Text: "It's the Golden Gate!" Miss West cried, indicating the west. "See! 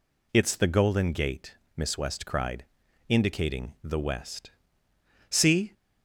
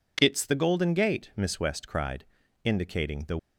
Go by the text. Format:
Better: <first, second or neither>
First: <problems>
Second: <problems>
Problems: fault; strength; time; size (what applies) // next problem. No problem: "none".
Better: first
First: none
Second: stops before "west See"; at 3.3 s